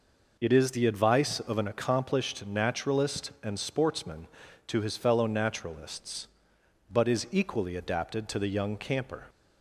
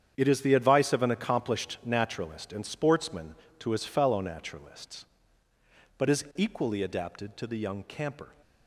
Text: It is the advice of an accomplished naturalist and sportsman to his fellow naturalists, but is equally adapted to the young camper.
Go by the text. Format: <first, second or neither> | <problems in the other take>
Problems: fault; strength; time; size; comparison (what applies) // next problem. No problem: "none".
first | gets quieter; strong; throughout; 11 dB